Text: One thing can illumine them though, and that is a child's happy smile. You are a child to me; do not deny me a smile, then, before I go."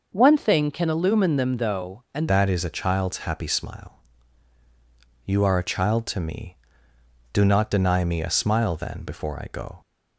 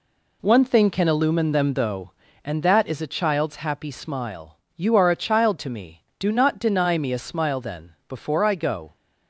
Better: second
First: changes voice at "that"; from 2.2 s on; 7.6 s long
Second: none

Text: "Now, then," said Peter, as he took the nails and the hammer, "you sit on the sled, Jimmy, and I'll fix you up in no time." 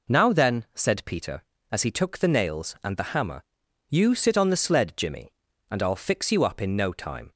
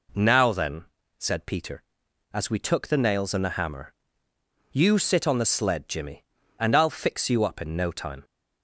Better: first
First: none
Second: says "we" for "he"; at 2.5 s

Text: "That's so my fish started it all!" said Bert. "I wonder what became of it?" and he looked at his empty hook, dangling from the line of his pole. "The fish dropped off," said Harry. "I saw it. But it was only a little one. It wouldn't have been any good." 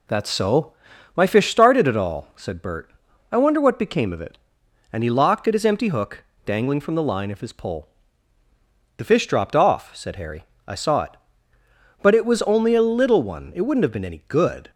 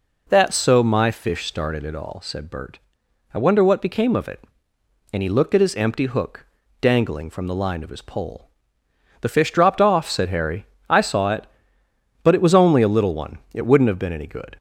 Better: second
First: pauses between "so" and "my"; at 0.7 s; 0.42 s long // says "locked" for "looked"; at 5.1 s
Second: none

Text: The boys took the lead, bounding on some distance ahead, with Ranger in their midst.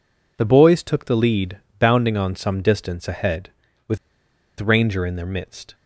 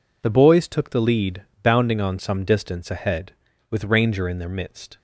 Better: second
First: pauses between "with" and "Ranger"; noticeable; at 3.9 s; 0.62 s long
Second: none

